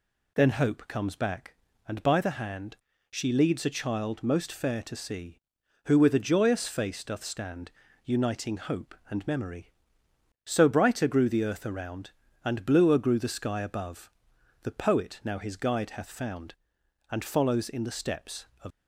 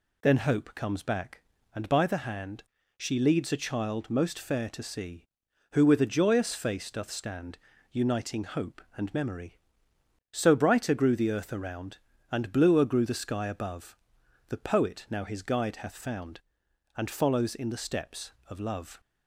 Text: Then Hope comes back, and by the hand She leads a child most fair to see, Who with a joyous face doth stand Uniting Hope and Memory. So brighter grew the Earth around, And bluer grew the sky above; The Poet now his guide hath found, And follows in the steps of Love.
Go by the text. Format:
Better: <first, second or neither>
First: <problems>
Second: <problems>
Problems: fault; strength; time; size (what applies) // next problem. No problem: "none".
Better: second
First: pauses between "hand" and "She"; slight; at 2.7 s; 0.34 s long // pauses between "stand" and "Uniting"; slight; at 7.6 s; 0.34 s long // stops before "Love"; at 18.7 s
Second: pauses between "hand" and "She"; slight; at 2.6 s; 0.34 s long // pauses between "stand" and "Uniting"; slight; at 7.5 s; 0.34 s long